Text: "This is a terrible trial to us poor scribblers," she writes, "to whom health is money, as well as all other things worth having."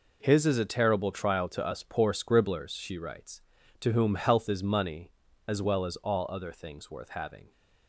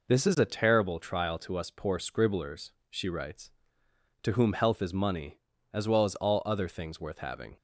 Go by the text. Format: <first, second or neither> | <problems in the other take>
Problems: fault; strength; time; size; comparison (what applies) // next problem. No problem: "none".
second | says "His" for "This"; at 0.2 s